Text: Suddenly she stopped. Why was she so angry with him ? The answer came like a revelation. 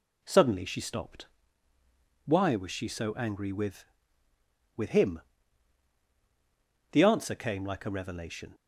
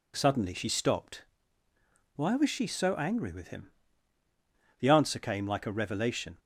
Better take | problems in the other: second | says "with" twice; at 4.7 s

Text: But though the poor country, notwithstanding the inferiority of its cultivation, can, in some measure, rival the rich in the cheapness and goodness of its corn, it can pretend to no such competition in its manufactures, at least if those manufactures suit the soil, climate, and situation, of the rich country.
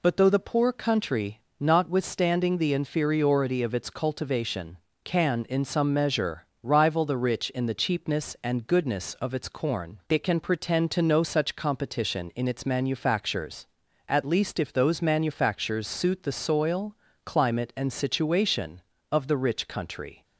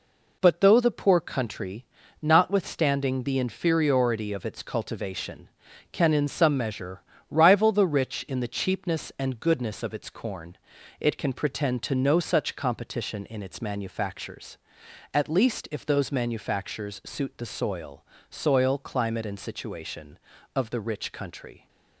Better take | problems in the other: first | says "soil" twice; at 18.2 s

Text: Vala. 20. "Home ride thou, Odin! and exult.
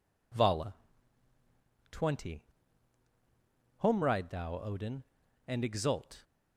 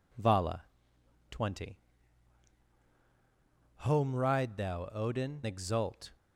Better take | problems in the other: first | skips "and"; at 5.4 s

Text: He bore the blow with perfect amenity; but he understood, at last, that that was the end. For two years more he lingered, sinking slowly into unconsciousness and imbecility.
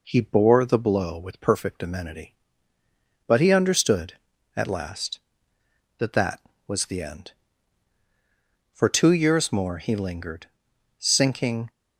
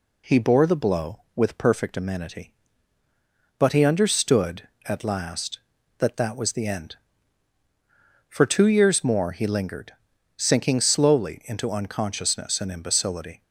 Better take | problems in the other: second | stops before "slowly into unconsciousness and imbecility"; at 11.6 s

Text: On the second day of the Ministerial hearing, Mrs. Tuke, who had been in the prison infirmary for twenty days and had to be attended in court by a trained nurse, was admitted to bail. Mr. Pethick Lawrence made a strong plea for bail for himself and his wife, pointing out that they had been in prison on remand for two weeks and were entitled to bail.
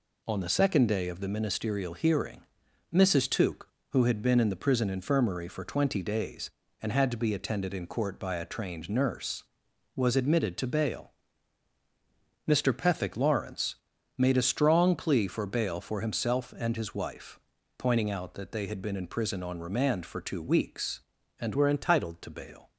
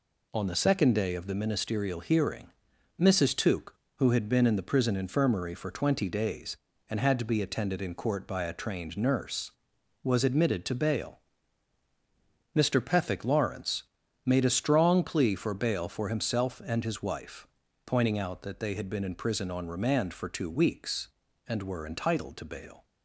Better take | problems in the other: second | pauses between "Lawrence" and "made"; at 13.7 s; 0.42 s long; also in the second // changes voice from "were" to "entitled"; from 21.5 to 22.2 s; 0.7 s long

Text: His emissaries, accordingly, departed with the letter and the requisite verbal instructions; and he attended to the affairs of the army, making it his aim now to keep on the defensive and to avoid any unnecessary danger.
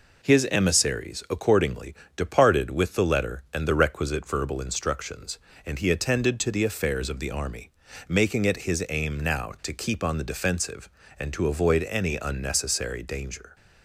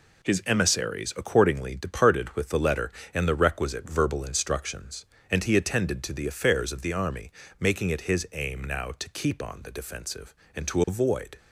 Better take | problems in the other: first | stops before "any unnecessary danger"; at 11.3 s

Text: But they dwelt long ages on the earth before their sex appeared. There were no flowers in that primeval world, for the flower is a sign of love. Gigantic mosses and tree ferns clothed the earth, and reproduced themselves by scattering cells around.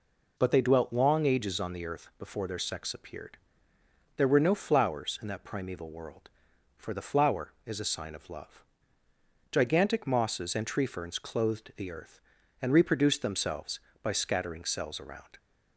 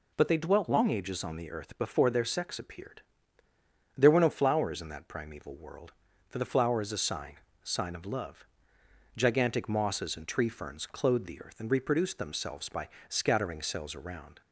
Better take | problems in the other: first | says "sign" twice; at 7.6 s // pauses between "by" and "scattering"; slight; at 12.8 s; 0.20 s long

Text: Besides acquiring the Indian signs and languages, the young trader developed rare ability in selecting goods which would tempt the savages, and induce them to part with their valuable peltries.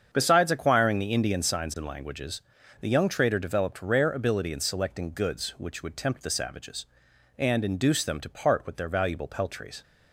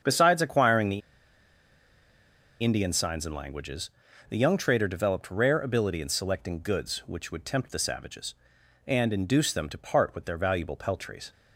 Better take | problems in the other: first | starts louder than the rest; strong; until 2.6 s; 7.5 dB; strong in the first // pauses between "the" and "Indian"; strong; at 1.0 s; 1.6 s long

